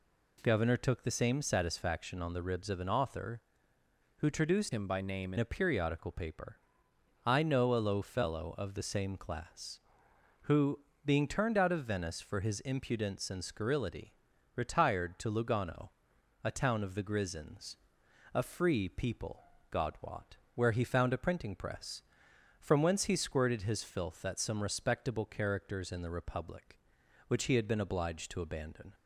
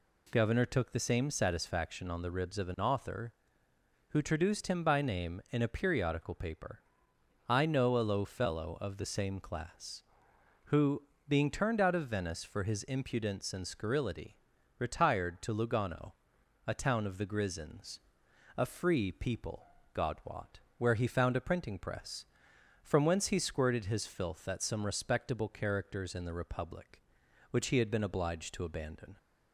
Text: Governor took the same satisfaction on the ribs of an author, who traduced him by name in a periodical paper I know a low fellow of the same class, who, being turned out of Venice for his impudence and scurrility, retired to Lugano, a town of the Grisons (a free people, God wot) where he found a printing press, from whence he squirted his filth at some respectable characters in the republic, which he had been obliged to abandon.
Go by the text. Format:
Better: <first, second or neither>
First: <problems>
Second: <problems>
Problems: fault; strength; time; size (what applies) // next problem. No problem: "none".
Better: second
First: changes voice from "him" to "in"; from 4.7 to 5.3 s; 0.6 s long // pauses between "paper" and "I"; noticeable; at 6.5 s; 0.68 s long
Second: pauses between "paper" and "I"; noticeable; at 6.8 s; 0.68 s long